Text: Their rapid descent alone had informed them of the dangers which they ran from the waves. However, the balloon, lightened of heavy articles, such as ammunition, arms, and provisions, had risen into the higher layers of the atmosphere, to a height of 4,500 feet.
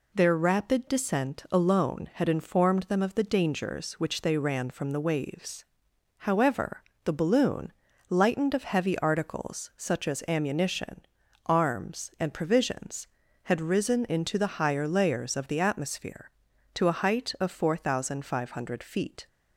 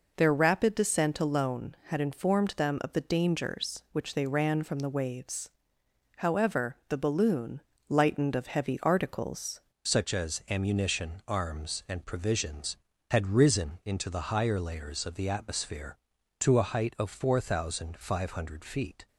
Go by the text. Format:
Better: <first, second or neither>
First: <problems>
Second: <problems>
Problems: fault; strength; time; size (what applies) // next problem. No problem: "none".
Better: first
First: none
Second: changes voice at "such"; from 9.8 s on; 9.2 s long